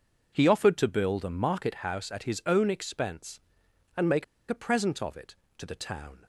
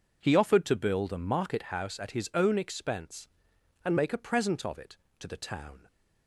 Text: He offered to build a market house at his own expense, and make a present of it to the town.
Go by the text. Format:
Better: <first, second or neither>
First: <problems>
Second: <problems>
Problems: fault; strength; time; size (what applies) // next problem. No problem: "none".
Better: second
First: pauses between "make" and "a"; slight; at 4.2 s; 0.24 s long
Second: none